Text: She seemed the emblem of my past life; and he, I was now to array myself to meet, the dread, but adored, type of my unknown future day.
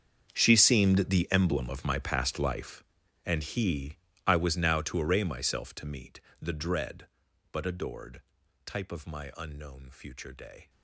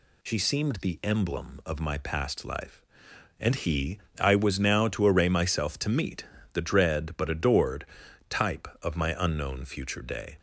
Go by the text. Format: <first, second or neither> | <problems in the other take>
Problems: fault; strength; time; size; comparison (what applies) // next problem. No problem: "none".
second | gets quieter; strong; throughout; 18 dB